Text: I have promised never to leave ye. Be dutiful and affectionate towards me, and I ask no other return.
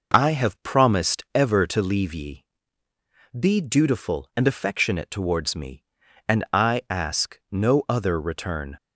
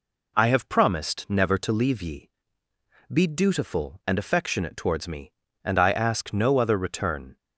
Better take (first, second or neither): second